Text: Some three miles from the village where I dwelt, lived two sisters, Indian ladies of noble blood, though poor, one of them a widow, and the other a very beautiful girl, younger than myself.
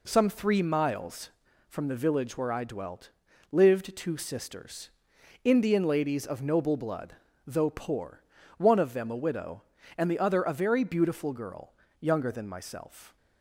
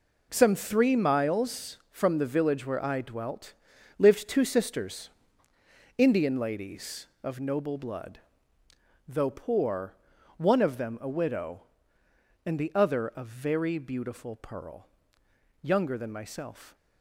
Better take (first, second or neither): first